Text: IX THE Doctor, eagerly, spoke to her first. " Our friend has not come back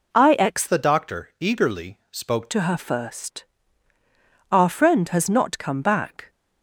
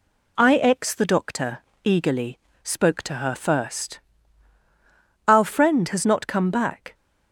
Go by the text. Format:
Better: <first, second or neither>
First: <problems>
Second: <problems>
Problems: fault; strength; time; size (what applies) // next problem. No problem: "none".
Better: second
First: changes voice from "THE" to "spoke"; from 0.6 to 2.4 s; 1.8 s long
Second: none